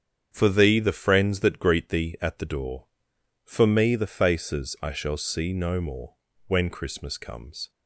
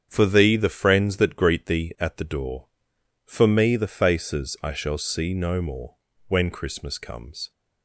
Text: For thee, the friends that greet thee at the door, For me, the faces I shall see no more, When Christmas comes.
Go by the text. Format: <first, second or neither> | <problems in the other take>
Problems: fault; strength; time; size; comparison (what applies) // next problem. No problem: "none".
neither | starts louder than the rest; strong; the same in both